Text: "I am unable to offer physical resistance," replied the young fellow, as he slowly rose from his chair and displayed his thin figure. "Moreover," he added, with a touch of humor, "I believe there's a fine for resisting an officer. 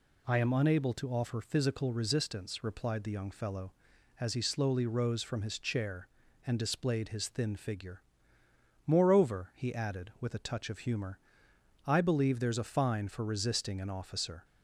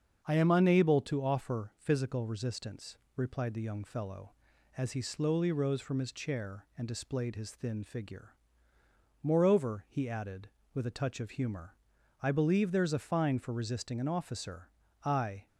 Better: first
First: none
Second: starts louder than the rest; until 1.2 s; 7 dB // goes on to say "I"; slight; from 15.0 s on; 0.44 s long

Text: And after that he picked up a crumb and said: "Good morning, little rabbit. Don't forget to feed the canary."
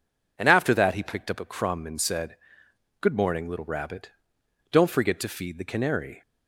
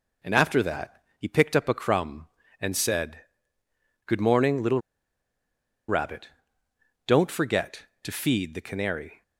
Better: first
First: none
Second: pauses between "that" and "he"; slight; at 1.0 s; 0.16 s long // pauses between "little" and "rabbit"; at 4.7 s; 1.0 s long

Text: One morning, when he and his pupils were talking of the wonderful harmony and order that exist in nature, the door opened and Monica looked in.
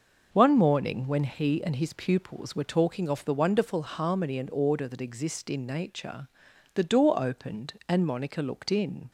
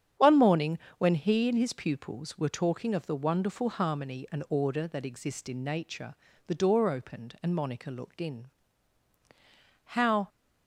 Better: first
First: starts louder than the rest; noticeable; until 1.3 s; 6 dB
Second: starts louder than the rest; strong; until 1.3 s; 8.5 dB // goes on to say "How"; slight; from 9.8 s on; 0.44 s long

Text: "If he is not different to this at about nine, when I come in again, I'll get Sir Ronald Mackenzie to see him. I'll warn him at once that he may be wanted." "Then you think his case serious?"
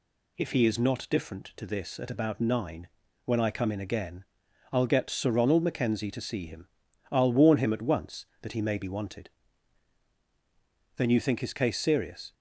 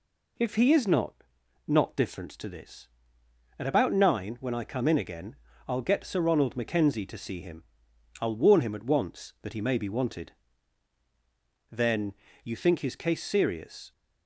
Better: first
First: none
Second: says "not" twice; at 1.6 s // pauses between "Then" and "you"; slight; at 12.1 s; 0.28 s long

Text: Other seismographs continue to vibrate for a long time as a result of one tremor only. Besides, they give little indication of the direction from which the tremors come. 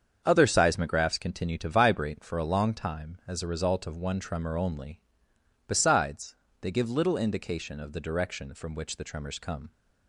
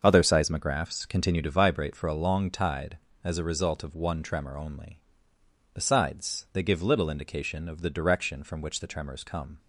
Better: first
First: starts louder than the rest; strong; until 1.2 s; 7.5 dB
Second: starts louder than the rest; until 1.0 s; 6.5 dB // says "tide" for "time"; at 2.4 s

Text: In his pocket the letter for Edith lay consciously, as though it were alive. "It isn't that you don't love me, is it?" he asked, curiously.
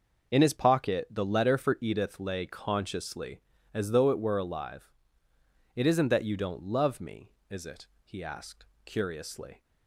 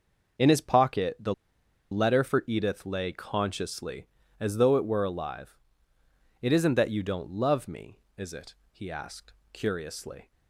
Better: first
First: none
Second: pauses between "the" and "letter"; noticeable; at 1.3 s; 0.57 s long

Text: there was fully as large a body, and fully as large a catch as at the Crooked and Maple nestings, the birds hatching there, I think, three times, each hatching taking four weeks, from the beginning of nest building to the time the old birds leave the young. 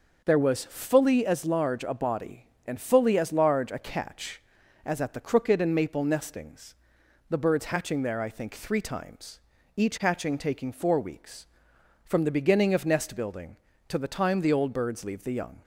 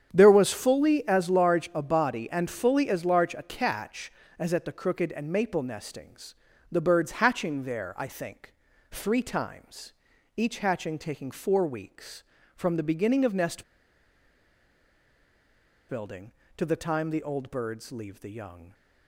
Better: first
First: none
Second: starts louder than the rest; strong; until 1.1 s; 8.5 dB // pauses between "nest" and "building"; strong; at 13.6 s; 2.2 s long

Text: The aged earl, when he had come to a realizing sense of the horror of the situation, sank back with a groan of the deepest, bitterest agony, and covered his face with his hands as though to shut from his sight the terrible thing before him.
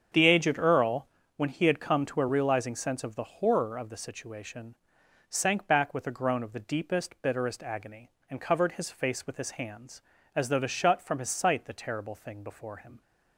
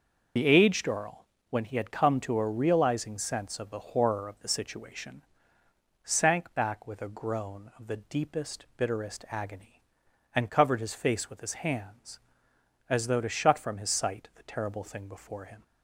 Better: first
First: starts louder than the rest; strong; until 1.4 s; 7.5 dB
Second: loses the start of "The"; at 0.3 s; 60 ms // starts louder than the rest; noticeable; until 1.6 s; 6 dB

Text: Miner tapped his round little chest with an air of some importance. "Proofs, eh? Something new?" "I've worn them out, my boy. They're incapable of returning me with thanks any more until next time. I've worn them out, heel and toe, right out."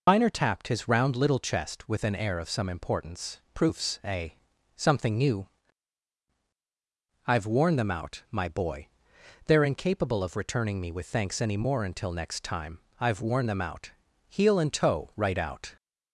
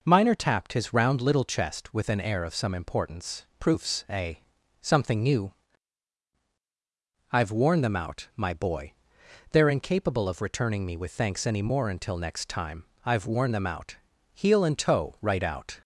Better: second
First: loses the start of "Miner"; at 0.0 s; 95 ms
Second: none

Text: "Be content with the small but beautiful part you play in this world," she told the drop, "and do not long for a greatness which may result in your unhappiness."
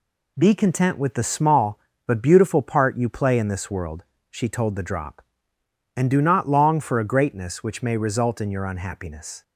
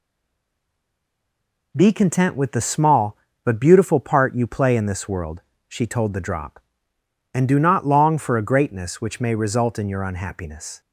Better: first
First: none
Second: stays silent before the first word; noticeable; until 1.7 s; 1.7 s long

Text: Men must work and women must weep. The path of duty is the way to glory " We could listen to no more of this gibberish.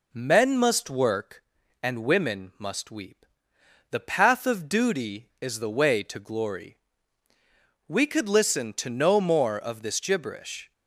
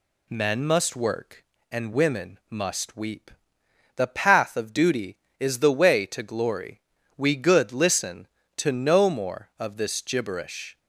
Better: first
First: none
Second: says "good" for "could"; at 7.3 s

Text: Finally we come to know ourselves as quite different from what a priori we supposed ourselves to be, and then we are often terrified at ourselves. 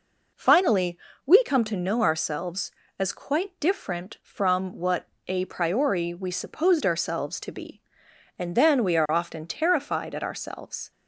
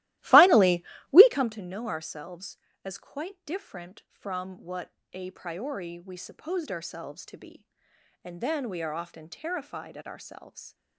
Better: first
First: pauses between "Finally" and "we"; slight; at 0.9 s; 0.28 s long // pauses between "what" and "a"; slight; at 5.0 s; 0.20 s long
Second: starts louder than the rest; strong; until 1.5 s; 16.5 dB // pauses between "Finally" and "we"; slight; at 0.8 s; 0.28 s long // pauses between "what" and "a"; slight; at 4.9 s; 0.20 s long

